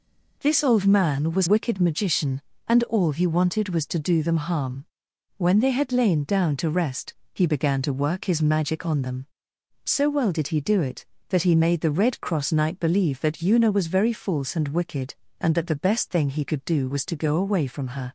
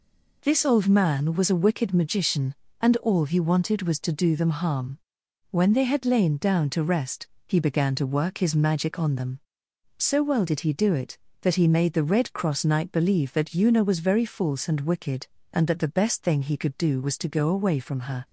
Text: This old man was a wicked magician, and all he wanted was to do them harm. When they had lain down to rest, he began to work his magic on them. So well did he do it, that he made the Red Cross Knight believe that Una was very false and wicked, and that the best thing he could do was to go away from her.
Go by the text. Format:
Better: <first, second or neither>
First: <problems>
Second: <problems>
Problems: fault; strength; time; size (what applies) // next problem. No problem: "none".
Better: second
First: skips "a"; at 1.4 s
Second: none